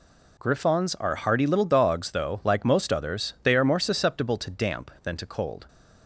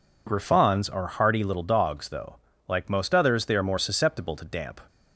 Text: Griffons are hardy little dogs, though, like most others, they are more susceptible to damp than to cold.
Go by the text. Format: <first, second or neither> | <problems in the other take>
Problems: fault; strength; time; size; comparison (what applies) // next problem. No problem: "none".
first | stops before "than to cold"; at 4.8 s